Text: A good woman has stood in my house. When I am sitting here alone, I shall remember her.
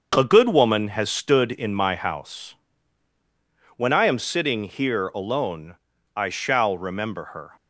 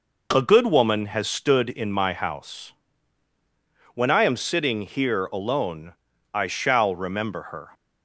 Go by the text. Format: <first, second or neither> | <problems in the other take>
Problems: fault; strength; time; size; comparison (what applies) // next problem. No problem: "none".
second | gets quieter; noticeable; throughout; 5 dB